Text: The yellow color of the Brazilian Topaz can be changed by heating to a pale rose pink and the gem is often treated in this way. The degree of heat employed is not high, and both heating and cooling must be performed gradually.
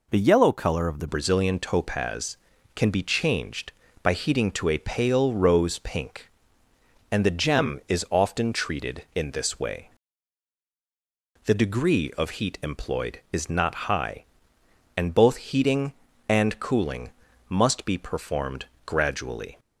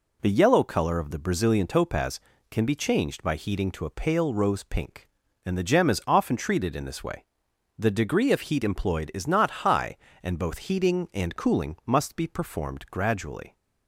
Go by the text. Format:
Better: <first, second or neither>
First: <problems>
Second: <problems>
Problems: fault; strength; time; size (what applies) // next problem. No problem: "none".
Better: second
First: changes voice at "Brazilian"; from 1.0 s on; 18.5 s long // pauses between "cooling" and "must"; at 17.0 s; 0.40 s long // pauses between "performed" and "gradually"; slight; at 18.6 s; 0.20 s long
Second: none